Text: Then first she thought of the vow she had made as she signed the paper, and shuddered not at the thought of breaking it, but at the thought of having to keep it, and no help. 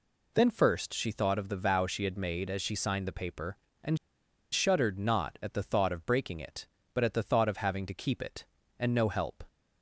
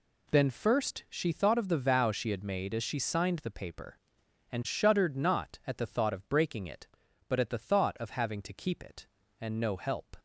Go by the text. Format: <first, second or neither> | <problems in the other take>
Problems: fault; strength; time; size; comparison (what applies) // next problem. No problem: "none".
second | pauses between "and" and "shuddered"; noticeable; at 3.9 s; 0.55 s long